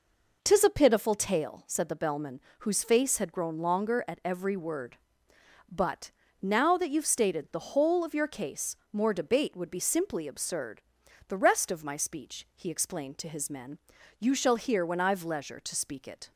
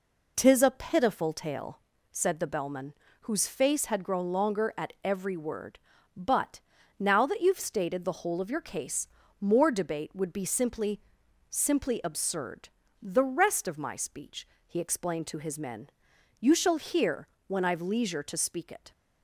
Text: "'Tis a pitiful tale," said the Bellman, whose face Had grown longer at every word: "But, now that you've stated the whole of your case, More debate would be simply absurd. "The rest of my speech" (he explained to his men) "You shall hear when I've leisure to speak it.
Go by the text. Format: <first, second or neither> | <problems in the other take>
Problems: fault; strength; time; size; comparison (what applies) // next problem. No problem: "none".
first | says "simply" twice; at 11.5 s // pauses between "hear" and "when"; slight; at 17.2 s; 0.18 s long